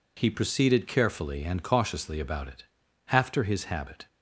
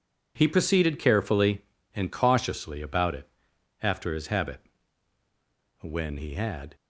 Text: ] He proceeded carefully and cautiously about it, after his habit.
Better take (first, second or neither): first